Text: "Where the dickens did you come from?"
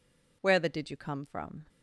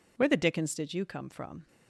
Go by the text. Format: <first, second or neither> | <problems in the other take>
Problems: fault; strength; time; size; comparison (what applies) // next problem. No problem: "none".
second | skips "dickens"; at 0.6 s